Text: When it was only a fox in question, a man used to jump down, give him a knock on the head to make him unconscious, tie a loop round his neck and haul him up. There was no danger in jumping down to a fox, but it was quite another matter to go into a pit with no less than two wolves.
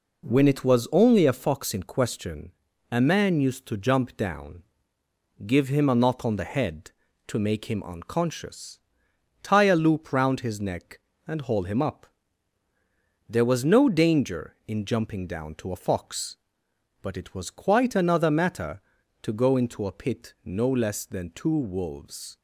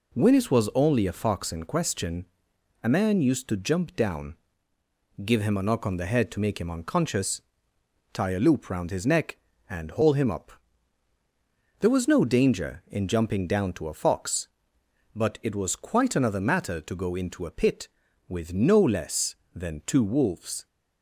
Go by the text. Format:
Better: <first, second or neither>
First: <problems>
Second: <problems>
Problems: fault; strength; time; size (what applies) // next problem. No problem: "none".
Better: second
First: skips "with"; at 20.3 s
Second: none